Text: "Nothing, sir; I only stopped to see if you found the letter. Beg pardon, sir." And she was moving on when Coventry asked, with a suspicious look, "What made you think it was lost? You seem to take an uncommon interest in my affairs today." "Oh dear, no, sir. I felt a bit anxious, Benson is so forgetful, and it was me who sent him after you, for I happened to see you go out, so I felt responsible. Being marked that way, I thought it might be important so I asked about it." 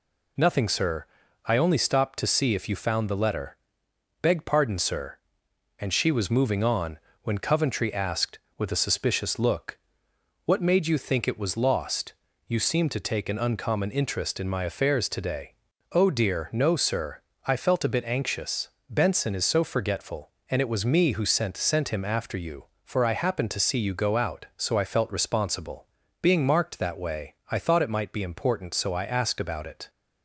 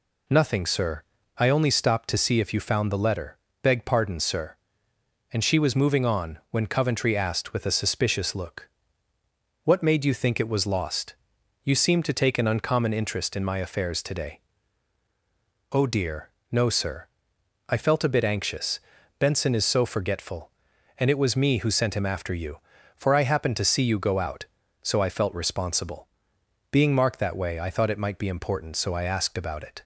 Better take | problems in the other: second | pauses between "on" and "when"; slight; at 6.9 s; 0.24 s long // says "sent" twice; at 21.5 s

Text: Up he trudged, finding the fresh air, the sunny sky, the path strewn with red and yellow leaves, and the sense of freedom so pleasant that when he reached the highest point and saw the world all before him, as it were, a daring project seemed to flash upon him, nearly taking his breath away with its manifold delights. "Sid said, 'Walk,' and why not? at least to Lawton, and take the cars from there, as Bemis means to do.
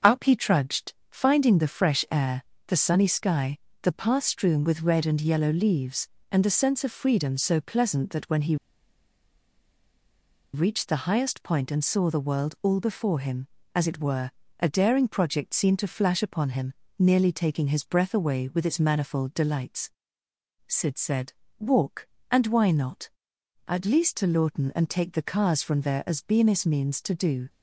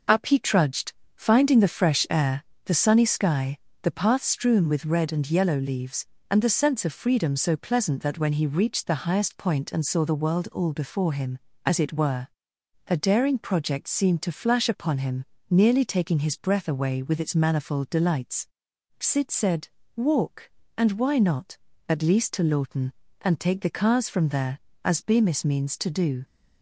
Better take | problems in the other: second | starts louder than the rest; until 1.2 s; 6.5 dB // pauses between "he" and "reached"; strong; at 8.5 s; 1.9 s long

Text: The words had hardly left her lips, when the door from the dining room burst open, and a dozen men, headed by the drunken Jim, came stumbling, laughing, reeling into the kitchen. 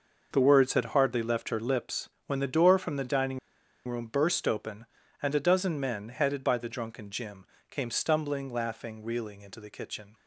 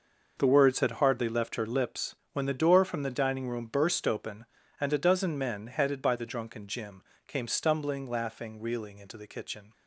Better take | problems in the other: second | pauses between "dining" and "room"; noticeable; at 3.3 s; 0.49 s long

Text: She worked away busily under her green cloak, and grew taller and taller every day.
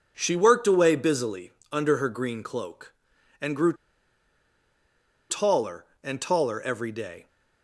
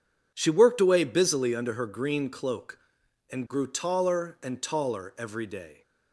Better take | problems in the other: second | pauses between "busily" and "under"; slight; at 1.5 s; 0.22 s long // pauses between "grew" and "taller"; strong; at 3.7 s; 1.5 s long

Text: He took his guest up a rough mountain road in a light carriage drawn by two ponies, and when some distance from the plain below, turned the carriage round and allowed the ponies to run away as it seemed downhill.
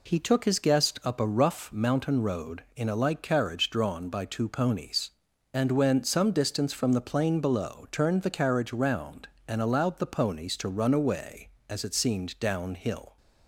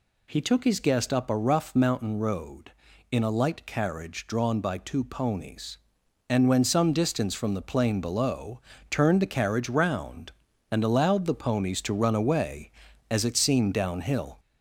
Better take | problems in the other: first | gets louder; slight; throughout; 3 dB

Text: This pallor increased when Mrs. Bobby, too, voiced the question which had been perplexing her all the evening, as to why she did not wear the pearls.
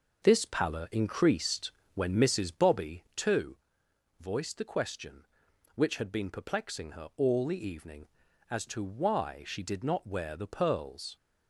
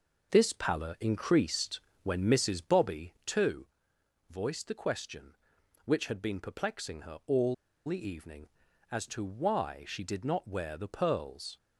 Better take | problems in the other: first | pauses between "increased" and "when"; slight; at 1.7 s; 0.24 s long; slight in the first // pauses between "all" and "the"; slight; at 7.5 s; 0.31 s long

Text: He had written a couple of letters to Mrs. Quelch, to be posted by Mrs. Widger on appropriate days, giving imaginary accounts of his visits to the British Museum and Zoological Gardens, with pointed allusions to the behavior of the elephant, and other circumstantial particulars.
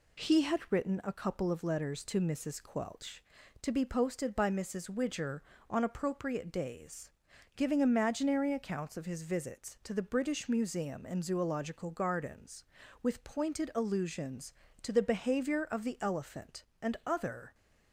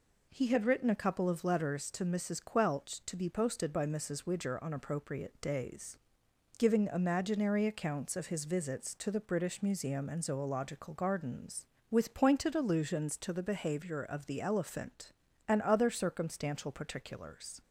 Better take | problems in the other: second | stops before "circumstantial particulars"; at 17.5 s

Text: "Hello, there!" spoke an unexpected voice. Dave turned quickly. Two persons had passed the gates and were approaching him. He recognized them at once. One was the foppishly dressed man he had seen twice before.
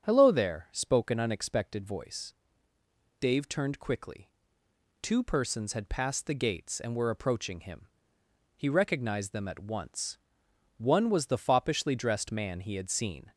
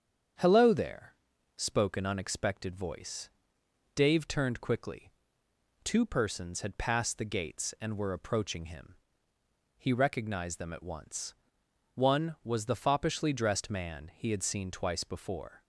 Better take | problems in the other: second | starts louder than the rest; strong; until 1.1 s; 7.5 dB; strong in the second // stops before "twice before"; at 13.3 s

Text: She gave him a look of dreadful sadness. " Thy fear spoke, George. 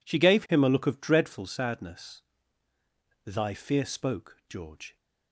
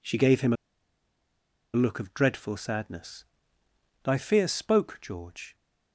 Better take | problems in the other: first | pauses between "a" and "look"; at 0.5 s; 1.2 s long

